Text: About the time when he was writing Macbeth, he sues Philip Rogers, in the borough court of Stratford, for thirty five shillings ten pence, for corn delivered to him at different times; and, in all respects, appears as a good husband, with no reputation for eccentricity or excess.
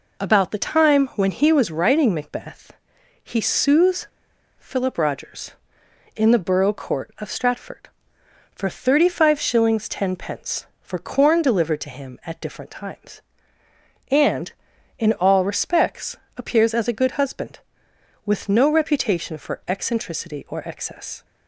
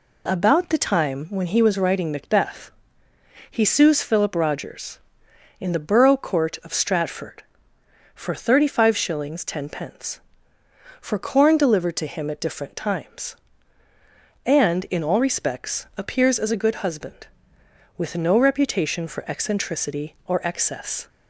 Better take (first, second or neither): second